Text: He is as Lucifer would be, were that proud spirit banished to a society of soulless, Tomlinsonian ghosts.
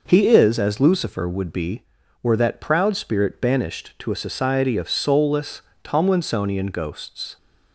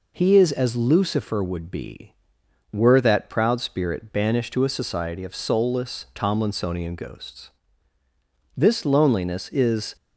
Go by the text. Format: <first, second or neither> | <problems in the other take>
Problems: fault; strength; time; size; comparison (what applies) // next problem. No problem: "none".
first | goes on to say "This loneliness is"; from 8.5 s on; 1.4 s long